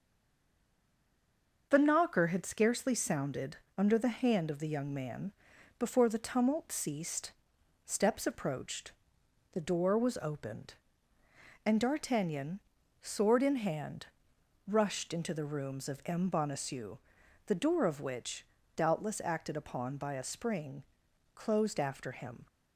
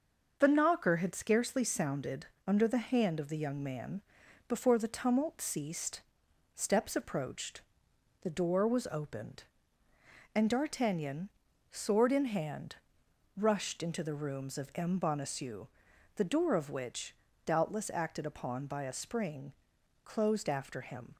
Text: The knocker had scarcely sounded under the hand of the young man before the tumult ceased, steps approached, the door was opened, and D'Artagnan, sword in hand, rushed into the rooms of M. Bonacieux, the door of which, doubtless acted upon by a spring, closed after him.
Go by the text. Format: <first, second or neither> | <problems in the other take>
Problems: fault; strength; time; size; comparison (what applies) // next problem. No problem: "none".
second | stays silent before the first word; noticeable; until 1.7 s; 1.7 s long // starts louder than the rest; until 2.7 s; 6.5 dB; also in the second // pauses between "sounded" and "under"; slight; at 3.5 s; 0.20 s long; slight in the second // pauses between "man" and "before"; noticeable; at 5.3 s; 0.46 s long; noticeable in the second